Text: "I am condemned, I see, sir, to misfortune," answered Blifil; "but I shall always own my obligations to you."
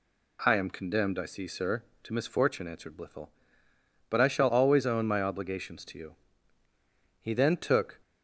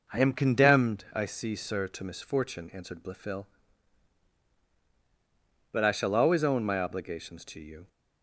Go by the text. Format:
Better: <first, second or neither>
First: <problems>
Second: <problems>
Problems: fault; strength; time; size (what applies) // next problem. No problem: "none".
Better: second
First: goes on to say "He then took"; noticeable; from 7.2 s on; 0.78 s long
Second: none